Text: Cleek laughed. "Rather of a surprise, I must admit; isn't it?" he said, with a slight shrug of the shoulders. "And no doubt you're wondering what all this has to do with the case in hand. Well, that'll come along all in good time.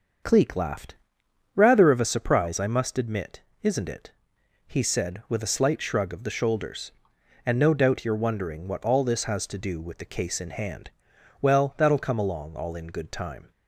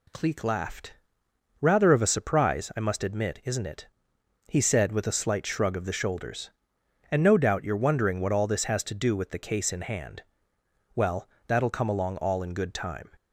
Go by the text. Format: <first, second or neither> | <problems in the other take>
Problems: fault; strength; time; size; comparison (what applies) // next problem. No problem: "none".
second | starts louder than the rest; until 2.1 s; 6.5 dB